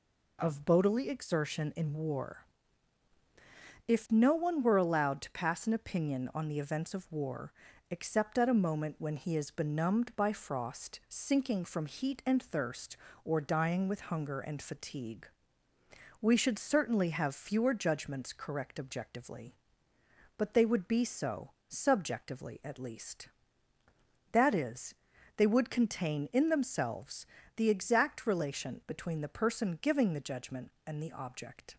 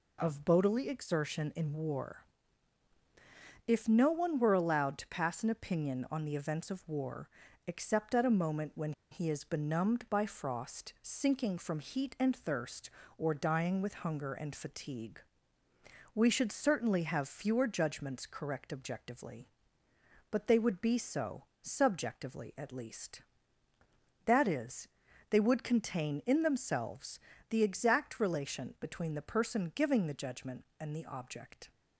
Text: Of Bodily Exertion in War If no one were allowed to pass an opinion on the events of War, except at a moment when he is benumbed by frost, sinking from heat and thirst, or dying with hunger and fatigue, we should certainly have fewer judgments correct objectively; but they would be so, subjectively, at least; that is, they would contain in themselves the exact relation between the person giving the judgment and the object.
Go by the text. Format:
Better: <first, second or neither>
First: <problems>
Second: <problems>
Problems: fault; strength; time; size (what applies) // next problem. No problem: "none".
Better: first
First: pauses between "War" and "If"; strong; at 2.4 s; 1.4 s long // pauses between "themselves" and "the"; slight; at 27.2 s; 0.30 s long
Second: pauses between "War" and "If"; strong; at 2.2 s; 1.4 s long // pauses between "when" and "he"; slight; at 8.9 s; 0.19 s long // pauses between "themselves" and "the"; slight; at 27.1 s; 0.30 s long